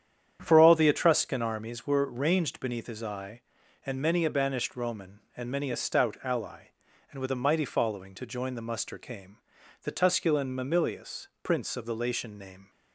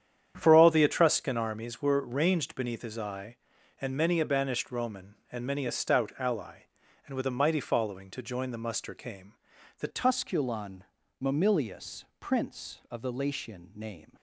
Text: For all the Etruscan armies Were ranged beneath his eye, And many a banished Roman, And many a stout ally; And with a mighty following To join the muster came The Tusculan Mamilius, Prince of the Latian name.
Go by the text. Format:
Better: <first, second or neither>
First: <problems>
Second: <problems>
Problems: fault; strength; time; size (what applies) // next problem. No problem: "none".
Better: first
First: starts louder than the rest; strong; until 1.4 s; 9 dB // pauses between "came" and "The"; noticeable; at 9.3 s; 0.46 s long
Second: starts louder than the rest; strong; until 1.3 s; 9 dB // pauses between "came" and "The"; noticeable; at 9.3 s; 0.46 s long // changes voice at "Tusculan"; from 9.9 s on; 4.2 s long // pauses between "Tusculan" and "Mamilius"; slight; at 10.8 s; 0.36 s long